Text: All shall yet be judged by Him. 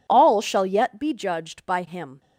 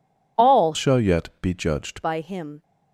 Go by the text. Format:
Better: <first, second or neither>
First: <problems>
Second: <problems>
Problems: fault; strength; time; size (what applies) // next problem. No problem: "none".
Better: first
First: none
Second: changes voice from "shall" to "judged"; from 0.7 to 2.0 s; 1.3 s long